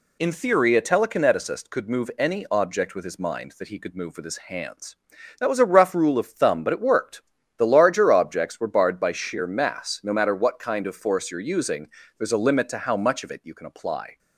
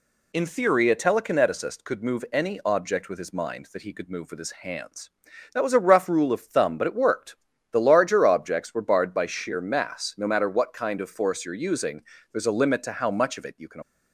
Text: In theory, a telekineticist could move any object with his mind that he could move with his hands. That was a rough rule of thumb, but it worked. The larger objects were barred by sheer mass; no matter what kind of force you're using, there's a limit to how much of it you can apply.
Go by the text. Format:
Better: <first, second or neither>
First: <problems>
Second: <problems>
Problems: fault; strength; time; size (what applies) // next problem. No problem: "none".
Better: first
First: none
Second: stops before "apply"; at 13.8 s